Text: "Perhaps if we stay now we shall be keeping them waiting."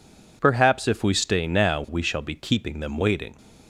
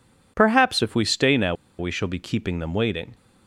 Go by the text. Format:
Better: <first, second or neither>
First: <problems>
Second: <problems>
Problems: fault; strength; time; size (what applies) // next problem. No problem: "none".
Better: first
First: none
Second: pauses between "now" and "we"; slight; at 1.5 s; 0.25 s long